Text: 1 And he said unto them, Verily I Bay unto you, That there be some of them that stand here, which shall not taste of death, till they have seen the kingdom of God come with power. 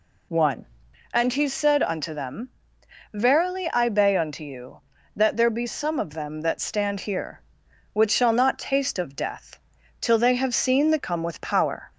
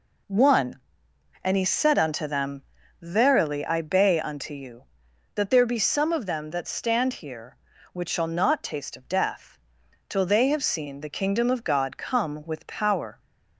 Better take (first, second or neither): second